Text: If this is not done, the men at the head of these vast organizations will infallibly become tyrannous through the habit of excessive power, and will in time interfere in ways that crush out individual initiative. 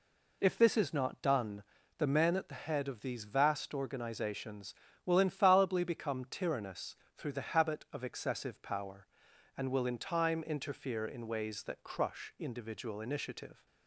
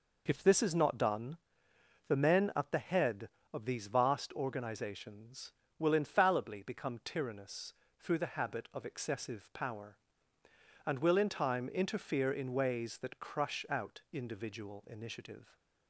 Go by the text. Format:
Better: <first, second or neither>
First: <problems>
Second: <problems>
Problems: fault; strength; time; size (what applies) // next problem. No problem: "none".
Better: second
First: pauses between "tyrannous" and "through"; slight; at 6.9 s; 0.22 s long // skips "out"; at 12.3 s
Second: pauses between "tyrannous" and "through"; slight; at 7.7 s; 0.28 s long